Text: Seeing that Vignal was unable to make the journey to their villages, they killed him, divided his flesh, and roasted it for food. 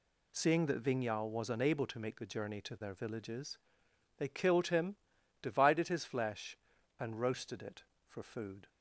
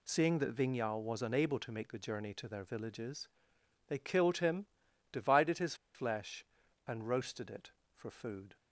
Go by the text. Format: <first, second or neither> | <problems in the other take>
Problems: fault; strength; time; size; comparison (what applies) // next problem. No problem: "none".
first | pauses between "his" and "flesh"; slight; at 5.7 s; 0.20 s long